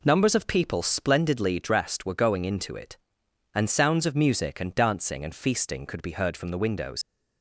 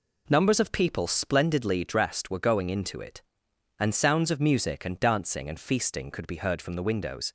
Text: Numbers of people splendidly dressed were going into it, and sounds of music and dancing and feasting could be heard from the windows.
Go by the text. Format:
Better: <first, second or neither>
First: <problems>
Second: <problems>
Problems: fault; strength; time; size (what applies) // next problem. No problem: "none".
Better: second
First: leaves "windows" unfinished; at 7.0 s; 60 ms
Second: none